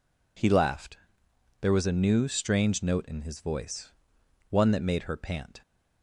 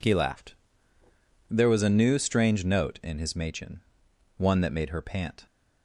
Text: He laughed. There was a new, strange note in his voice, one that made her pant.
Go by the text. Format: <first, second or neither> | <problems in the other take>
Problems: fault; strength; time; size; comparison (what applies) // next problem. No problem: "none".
first | says "machin" for "voice"; at 3.3 s